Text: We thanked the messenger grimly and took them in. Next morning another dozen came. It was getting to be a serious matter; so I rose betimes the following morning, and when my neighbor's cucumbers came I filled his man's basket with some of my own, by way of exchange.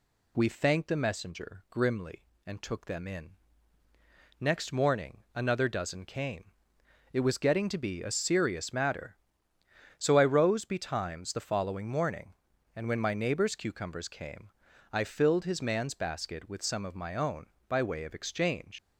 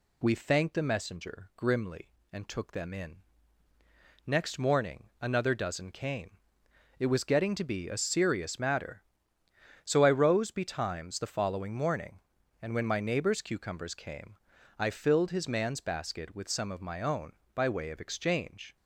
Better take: second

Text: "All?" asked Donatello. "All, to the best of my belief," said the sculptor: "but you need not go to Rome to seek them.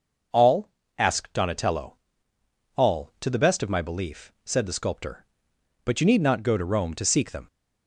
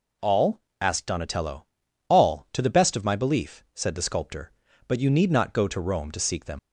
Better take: first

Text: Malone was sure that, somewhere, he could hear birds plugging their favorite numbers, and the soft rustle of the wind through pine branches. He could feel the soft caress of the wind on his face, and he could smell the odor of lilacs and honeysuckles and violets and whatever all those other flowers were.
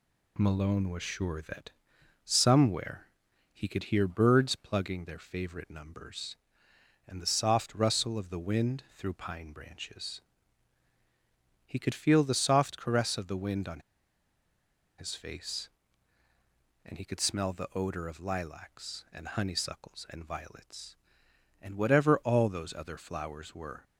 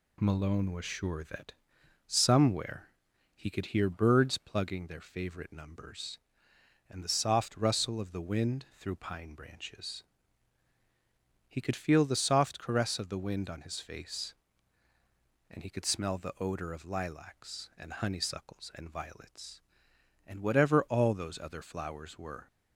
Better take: second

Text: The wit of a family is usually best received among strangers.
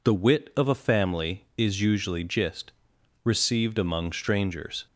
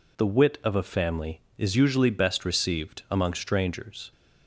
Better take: second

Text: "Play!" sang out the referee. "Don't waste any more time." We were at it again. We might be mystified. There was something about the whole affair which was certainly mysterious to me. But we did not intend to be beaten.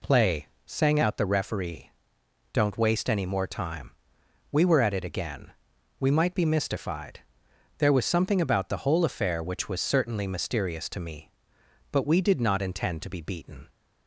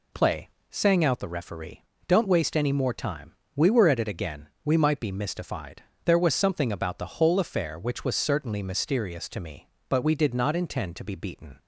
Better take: neither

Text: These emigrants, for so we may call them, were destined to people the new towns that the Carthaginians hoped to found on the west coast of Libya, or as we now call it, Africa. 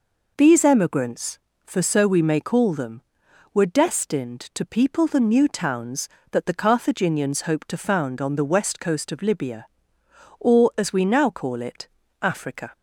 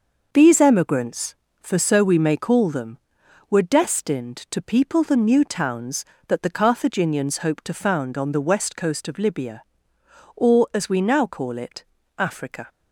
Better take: first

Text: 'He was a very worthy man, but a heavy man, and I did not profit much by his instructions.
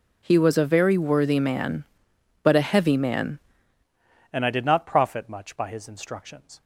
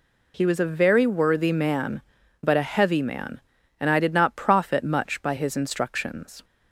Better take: second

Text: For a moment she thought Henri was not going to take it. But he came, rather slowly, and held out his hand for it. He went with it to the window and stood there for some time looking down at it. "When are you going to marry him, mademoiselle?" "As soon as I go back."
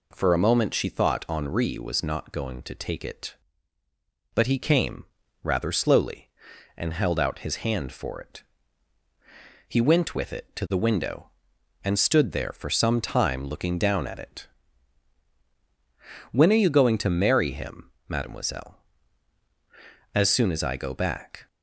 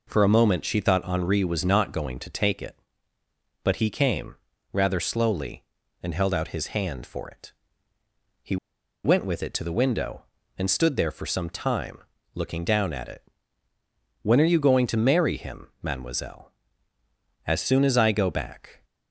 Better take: first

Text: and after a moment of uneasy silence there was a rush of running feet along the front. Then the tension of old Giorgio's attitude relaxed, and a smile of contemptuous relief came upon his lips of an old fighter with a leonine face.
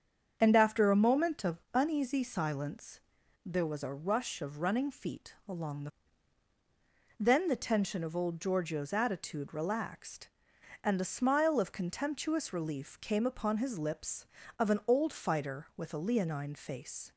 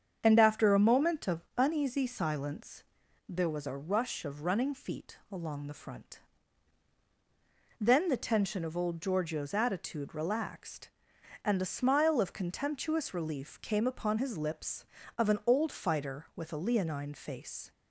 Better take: second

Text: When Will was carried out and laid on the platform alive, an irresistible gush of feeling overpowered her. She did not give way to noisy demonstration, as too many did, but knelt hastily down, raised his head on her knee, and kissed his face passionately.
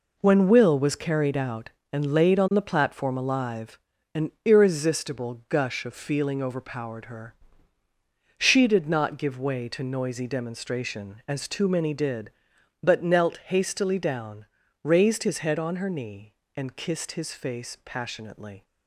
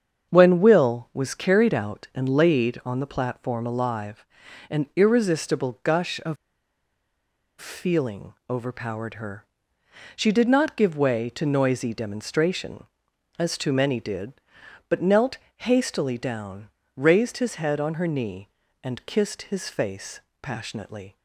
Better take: first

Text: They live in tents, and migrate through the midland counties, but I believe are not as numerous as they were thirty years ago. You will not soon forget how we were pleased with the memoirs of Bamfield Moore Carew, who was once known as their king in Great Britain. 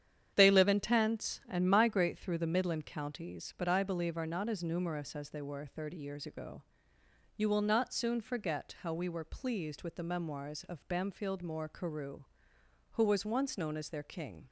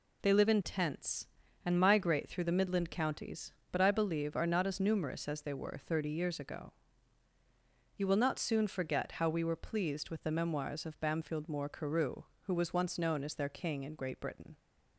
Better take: second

